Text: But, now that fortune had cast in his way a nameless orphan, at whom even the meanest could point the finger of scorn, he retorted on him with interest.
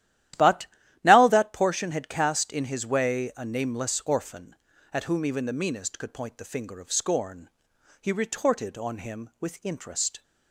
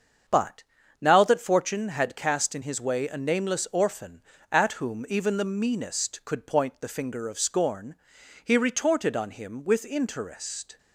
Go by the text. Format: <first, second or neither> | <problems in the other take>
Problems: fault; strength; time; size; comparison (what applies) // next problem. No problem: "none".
second | starts louder than the rest; strong; until 1.7 s; 13 dB; also in the second // says "portion" for "fortune"; at 1.5 s